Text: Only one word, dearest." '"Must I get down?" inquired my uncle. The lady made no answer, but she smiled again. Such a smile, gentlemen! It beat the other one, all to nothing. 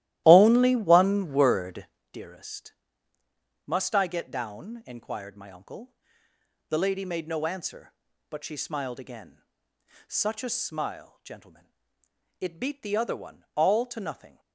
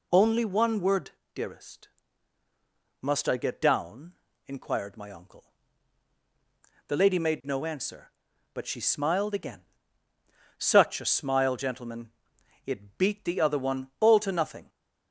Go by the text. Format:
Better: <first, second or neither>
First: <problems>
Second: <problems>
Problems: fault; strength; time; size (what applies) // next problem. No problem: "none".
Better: second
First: starts louder than the rest; strong; until 2.1 s; 14.5 dB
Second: none